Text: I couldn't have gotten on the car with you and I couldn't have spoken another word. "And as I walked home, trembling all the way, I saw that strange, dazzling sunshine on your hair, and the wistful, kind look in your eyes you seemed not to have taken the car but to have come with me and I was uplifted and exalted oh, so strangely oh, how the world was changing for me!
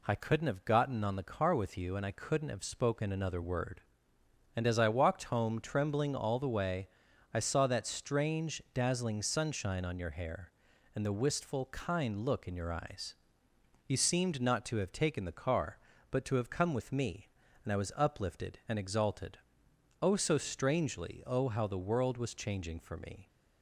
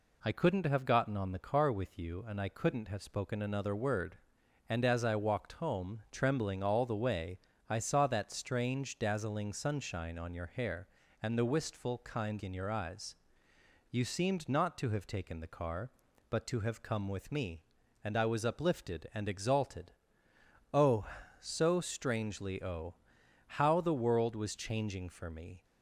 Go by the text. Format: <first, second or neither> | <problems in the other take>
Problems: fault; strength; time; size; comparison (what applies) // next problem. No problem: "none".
first | skips "look"; at 12.4 s // pauses between "eyes" and "you"; noticeable; at 13.1 s; 0.74 s long; noticeable in the first // pauses between "exalted" and "oh"; noticeable; at 19.9 s; 0.80 s long; noticeable in the first